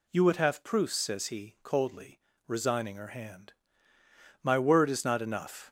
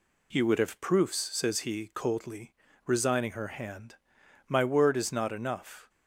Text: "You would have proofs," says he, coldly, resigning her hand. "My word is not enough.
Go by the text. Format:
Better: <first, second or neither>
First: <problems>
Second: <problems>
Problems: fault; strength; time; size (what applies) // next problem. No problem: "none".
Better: second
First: gets louder; slight; throughout; 3 dB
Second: none